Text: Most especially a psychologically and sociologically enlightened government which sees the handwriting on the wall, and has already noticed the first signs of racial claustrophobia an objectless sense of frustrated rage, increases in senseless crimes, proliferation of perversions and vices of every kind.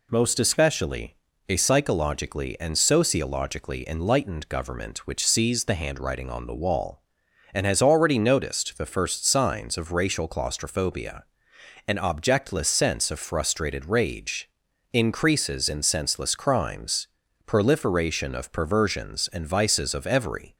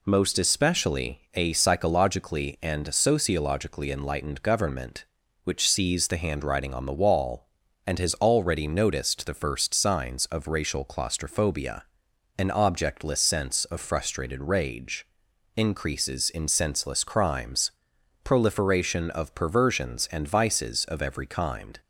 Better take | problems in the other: second | pauses between "especially" and "a"; slight; at 1.1 s; 0.32 s long // pauses between "claustrophobia" and "an"; noticeable; at 11.2 s; 0.64 s long; noticeable in the second // stops before "kind"; at 20.5 s

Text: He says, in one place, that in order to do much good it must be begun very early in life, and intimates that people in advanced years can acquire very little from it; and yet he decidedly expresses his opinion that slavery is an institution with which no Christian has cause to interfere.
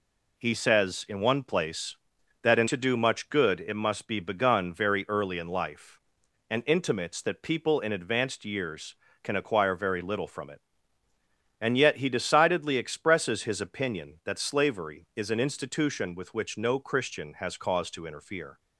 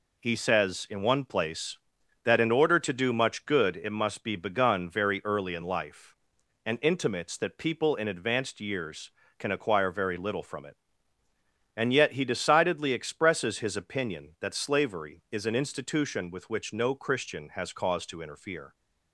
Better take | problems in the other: second | skips "order"; at 2.6 s

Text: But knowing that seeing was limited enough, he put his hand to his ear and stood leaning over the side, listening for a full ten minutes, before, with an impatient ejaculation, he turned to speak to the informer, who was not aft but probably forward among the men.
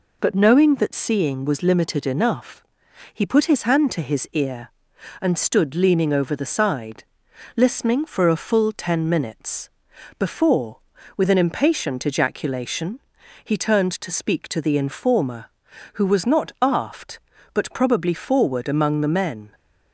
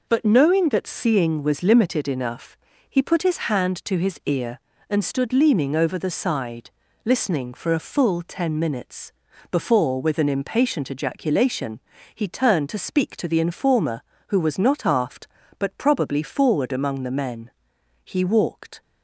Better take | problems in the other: first | goes on to say "He walked"; noticeable; from 18.0 s on; 0.78 s long

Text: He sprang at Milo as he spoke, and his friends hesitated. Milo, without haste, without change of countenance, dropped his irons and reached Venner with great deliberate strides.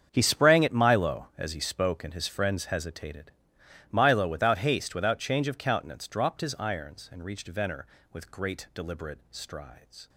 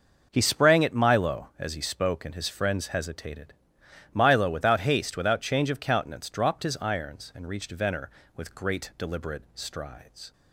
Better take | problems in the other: second | gets quieter; strong; throughout; 15 dB

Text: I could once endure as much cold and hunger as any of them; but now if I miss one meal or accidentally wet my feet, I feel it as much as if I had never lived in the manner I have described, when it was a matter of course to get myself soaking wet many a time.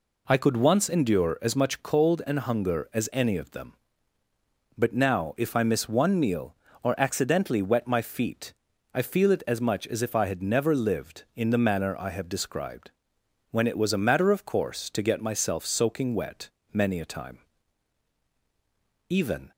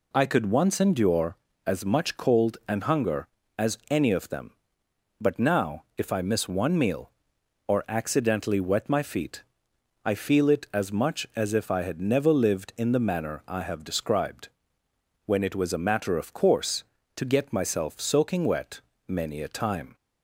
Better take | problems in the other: second | pauses between "wet" and "many"; slight; at 16.4 s; 0.24 s long; slight in the second // goes on to say "Even"; slight; from 19.0 s on; 0.42 s long

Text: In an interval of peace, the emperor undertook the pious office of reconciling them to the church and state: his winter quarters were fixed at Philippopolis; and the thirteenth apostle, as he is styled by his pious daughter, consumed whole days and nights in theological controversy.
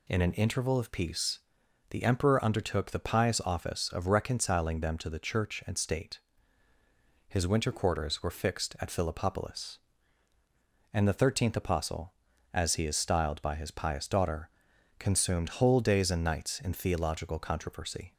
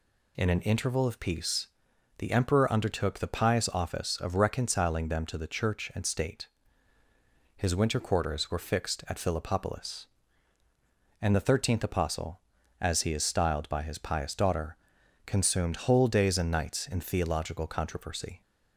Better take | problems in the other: neither | none

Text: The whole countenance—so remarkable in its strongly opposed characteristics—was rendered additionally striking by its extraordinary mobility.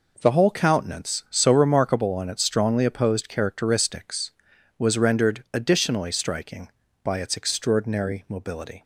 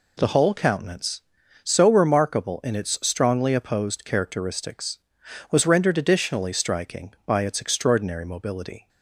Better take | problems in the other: second | says "on" for "in"; at 2.1 s

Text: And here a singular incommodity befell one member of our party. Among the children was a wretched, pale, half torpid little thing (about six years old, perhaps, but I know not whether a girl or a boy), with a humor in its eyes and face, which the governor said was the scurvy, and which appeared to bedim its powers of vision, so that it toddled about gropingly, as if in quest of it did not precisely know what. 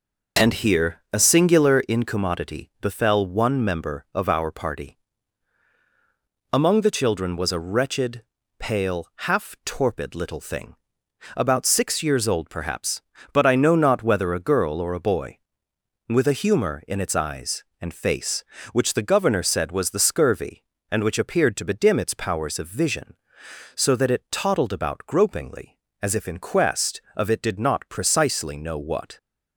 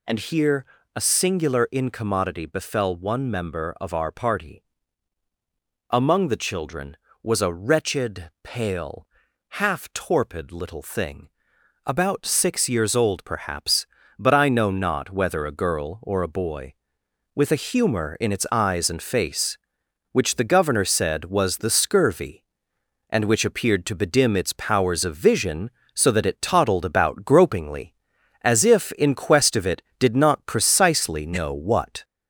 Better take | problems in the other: first | gets louder; slight; throughout; 3 dB // pauses between "here" and "a"; slight; at 0.6 s; 0.28 s long

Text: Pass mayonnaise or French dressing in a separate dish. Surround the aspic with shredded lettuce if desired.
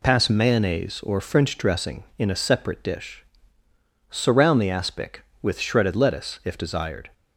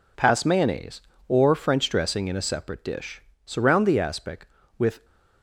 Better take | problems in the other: first | stops before "shredded lettuce if desired"; at 5.0 s

